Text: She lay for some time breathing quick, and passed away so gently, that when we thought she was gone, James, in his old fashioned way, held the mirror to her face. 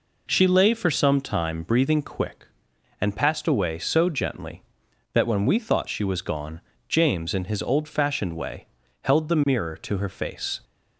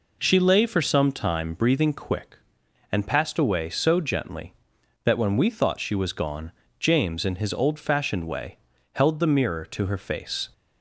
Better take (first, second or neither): neither